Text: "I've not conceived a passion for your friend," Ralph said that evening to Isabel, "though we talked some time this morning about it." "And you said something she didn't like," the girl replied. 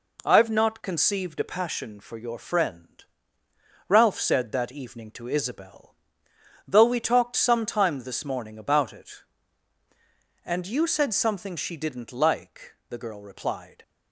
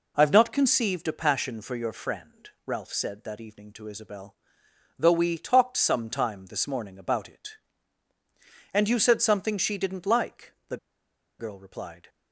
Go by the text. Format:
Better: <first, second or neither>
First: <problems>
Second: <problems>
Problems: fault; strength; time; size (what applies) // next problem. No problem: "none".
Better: first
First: none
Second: pauses between "the" and "girl"; noticeable; at 10.7 s; 0.62 s long